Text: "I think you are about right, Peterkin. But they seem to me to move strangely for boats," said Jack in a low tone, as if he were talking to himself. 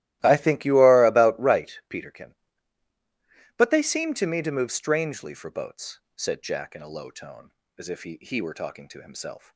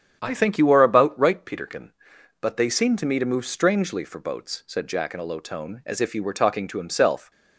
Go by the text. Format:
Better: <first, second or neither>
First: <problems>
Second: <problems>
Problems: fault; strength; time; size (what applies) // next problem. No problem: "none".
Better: second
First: starts louder than the rest; strong; until 1.2 s; 15 dB // says "he" twice; at 8.1 s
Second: starts louder than the rest; strong; until 1.2 s; 8.5 dB